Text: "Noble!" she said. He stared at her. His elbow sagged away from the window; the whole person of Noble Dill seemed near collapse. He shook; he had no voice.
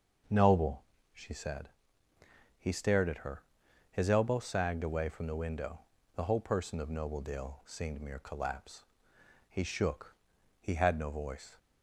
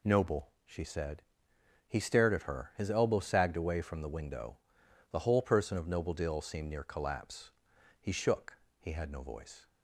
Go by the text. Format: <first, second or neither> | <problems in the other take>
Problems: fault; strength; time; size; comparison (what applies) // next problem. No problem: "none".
second | starts louder than the rest; until 1.5 s; 6.5 dB // says "mere" for "near"; at 7.9 s